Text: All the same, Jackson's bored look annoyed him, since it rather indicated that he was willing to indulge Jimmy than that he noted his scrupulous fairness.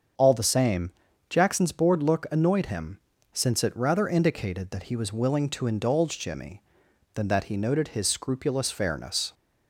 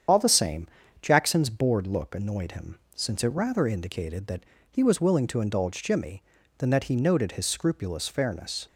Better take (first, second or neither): first